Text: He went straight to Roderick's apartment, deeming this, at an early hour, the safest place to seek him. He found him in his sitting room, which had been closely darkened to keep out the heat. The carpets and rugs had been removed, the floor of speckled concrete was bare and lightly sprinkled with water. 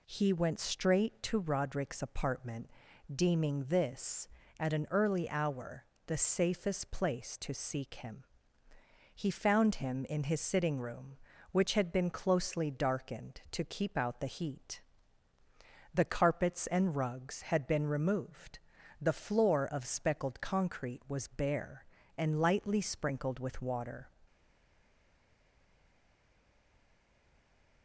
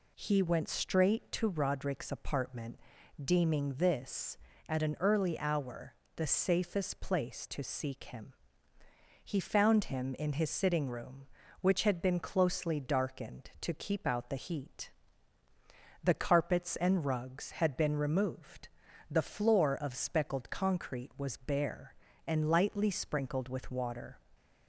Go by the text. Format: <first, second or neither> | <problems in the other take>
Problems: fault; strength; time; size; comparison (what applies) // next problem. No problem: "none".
second | stays silent after the last word; strong; from 24.2 s on; 3.6 s long